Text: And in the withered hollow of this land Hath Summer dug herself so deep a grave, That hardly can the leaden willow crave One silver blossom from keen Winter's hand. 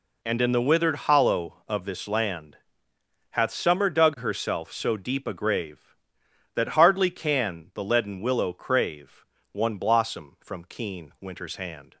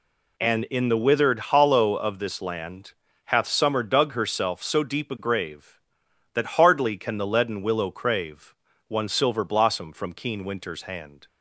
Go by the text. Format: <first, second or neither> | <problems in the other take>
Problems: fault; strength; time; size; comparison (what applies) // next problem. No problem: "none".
second | pauses between "land" and "Hath"; noticeable; at 2.5 s; 0.74 s long; slight in the second // pauses between "crave" and "One"; slight; at 9.2 s; 0.26 s long; slight in the second // skips "silver"; at 9.7 s